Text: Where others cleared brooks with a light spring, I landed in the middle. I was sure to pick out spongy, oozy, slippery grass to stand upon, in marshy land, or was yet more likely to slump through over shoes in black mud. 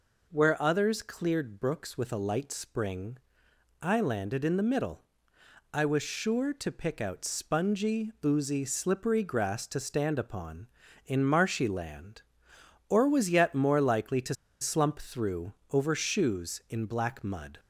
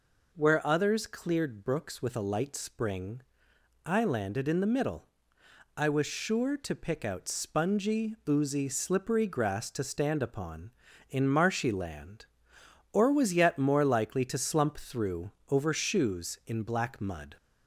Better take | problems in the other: second | pauses between "to" and "slump"; slight; at 14.3 s; 0.27 s long // pauses between "through" and "over"; slight; at 15.5 s; 0.18 s long; slight in the second

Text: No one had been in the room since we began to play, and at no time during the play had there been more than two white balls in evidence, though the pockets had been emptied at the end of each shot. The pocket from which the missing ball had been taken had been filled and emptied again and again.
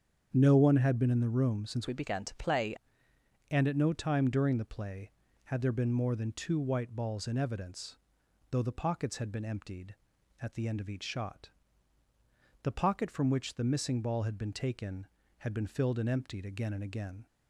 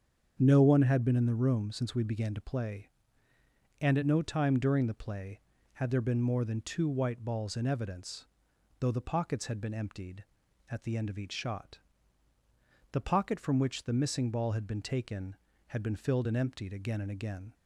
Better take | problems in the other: second | starts louder than the rest; strong; until 1.3 s; 7.5 dB; strong in the second // changes voice from "we" to "play"; from 1.8 to 2.7 s; 0.9 s long

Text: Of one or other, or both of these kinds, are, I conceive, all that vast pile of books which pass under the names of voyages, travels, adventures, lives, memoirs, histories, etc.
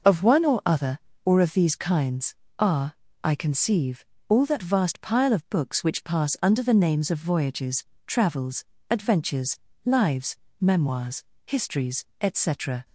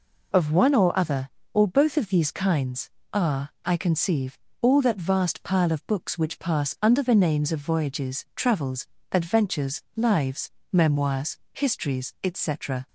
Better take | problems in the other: second | skips "both"; at 1.3 s

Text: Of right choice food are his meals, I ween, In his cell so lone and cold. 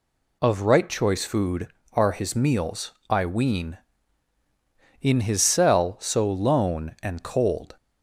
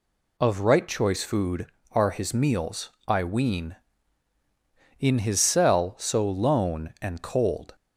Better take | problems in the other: neither | none

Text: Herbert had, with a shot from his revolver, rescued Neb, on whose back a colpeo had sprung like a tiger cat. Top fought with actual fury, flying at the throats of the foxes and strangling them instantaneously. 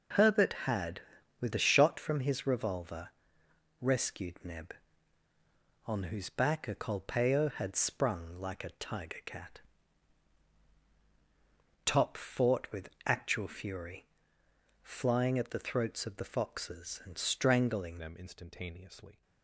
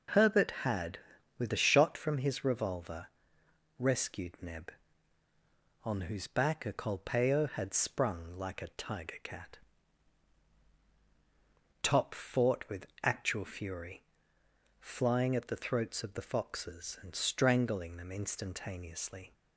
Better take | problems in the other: second | pauses between "with" and "actual"; slight; at 12.8 s; 0.16 s long; slight in the second // changes voice at "them"; from 17.9 s on; 1.3 s long

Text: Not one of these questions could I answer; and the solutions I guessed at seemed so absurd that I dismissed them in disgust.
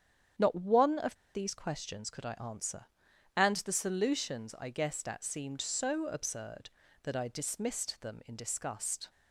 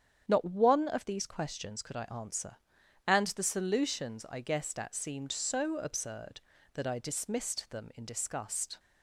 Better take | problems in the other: second | starts louder than the rest; strong; until 1.5 s; 8.5 dB; strong in the second // pauses between "of" and "these"; slight; at 1.1 s; 0.19 s long

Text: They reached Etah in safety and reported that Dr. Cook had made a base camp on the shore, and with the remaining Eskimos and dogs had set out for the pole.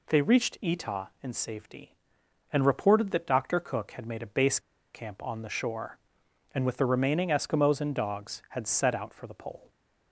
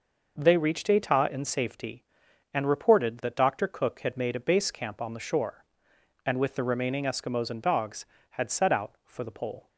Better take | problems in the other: second | pauses between "base" and "camp"; slight; at 4.5 s; 0.34 s long

